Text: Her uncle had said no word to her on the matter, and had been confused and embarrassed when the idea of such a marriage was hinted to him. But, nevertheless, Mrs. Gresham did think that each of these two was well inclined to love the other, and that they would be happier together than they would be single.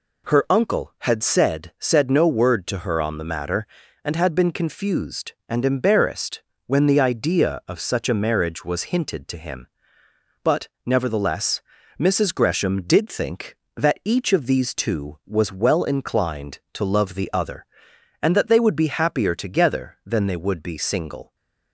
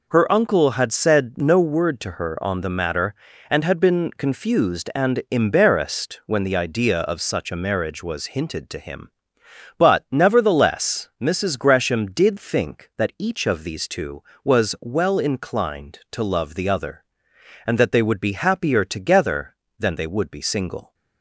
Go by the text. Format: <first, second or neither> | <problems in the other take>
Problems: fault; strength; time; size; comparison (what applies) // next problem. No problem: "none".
second | says "said" twice; at 1.7 s // pauses between "embarrassed" and "when"; slight; at 6.4 s; 0.24 s long // stays silent after the last word; slight; from 21.2 s on; 0.5 s long